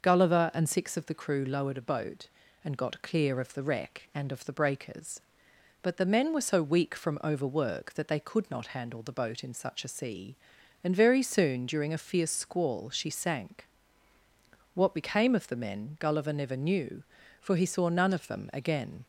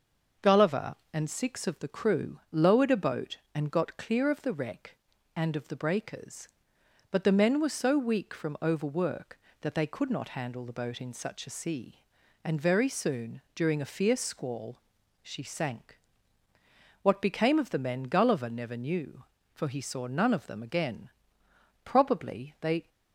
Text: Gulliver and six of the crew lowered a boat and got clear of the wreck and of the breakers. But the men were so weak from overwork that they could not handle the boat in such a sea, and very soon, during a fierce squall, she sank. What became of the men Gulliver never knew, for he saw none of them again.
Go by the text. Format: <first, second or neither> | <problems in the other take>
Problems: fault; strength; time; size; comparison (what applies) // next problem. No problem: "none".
first | starts louder than the rest; until 1.5 s; 6.5 dB; noticeable in the first // goes on to say "Probably they"; noticeable; from 21.8 s on; 1.0 s long